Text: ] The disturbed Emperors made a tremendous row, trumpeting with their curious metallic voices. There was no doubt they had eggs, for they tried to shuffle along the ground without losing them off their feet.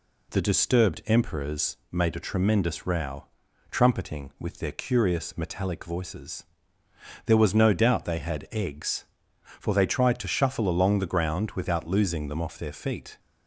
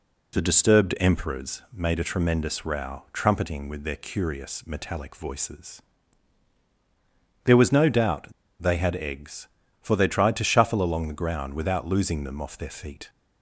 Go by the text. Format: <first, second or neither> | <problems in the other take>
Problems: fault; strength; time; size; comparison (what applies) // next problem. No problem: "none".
first | pauses between "doubt" and "they"; slight; at 8.3 s; 0.28 s long